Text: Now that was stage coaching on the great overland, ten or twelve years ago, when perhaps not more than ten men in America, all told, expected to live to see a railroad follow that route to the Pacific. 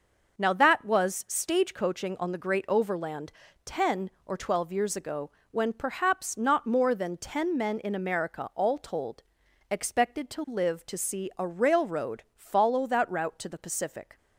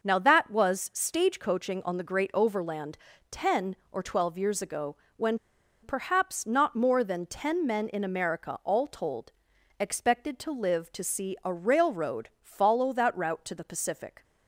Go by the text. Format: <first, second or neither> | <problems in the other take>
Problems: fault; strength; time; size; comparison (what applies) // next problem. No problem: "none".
first | pauses between "when" and "perhaps"; at 5.3 s; 0.45 s long